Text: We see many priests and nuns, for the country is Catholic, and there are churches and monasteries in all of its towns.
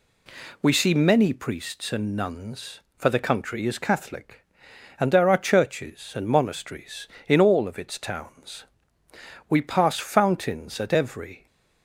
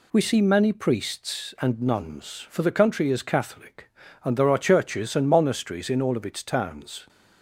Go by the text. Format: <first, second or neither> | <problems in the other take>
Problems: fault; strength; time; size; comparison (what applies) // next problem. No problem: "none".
second | goes on to say "We pass fountains at every"; strong; from 9.4 s on; 1.9 s long